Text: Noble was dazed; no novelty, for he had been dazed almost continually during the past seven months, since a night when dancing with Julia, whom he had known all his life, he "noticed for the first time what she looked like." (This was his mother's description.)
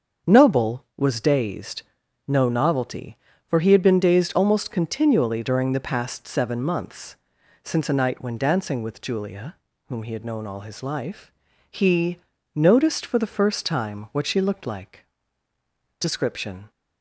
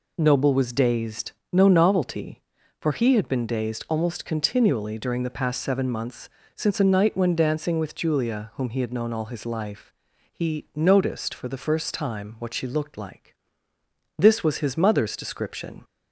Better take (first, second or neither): second